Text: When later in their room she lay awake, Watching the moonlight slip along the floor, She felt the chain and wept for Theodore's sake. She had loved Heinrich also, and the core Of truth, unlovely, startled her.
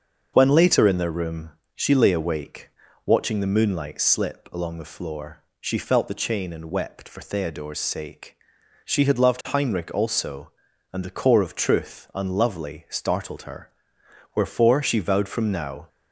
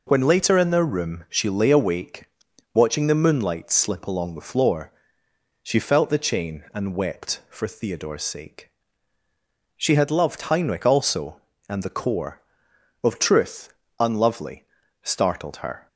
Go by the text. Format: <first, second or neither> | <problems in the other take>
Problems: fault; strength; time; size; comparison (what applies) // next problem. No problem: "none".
second | starts louder than the rest; until 1.3 s; 6.5 dB // pauses between "room" and "she"; slight; at 1.5 s; 0.26 s long // goes on to say "Wherefore She vowed from now"; from 14.3 s on; 1.5 s long